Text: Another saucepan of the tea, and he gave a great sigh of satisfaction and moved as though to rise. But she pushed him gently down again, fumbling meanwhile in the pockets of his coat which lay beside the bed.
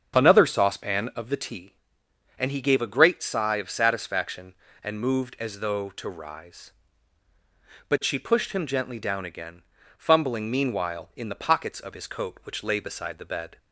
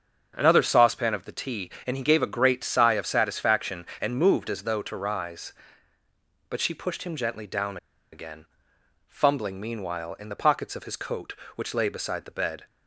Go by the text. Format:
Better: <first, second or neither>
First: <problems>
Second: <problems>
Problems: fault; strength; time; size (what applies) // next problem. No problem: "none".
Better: first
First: starts louder than the rest; strong; until 1.2 s; 7.5 dB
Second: starts louder than the rest; until 1.3 s; 7 dB // pauses between "down" and "again"; slight; at 7.7 s; 0.36 s long